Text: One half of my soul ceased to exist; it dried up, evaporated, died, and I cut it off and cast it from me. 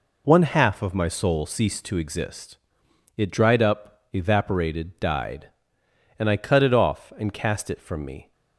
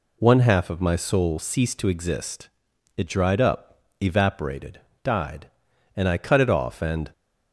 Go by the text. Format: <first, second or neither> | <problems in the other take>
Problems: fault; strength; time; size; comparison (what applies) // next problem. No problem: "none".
first | stops before "cast it from me"; at 7.1 s